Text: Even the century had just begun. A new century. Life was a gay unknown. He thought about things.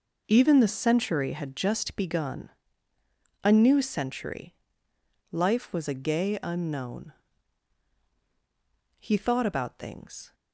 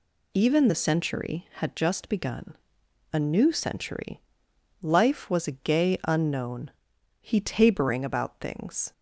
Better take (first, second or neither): first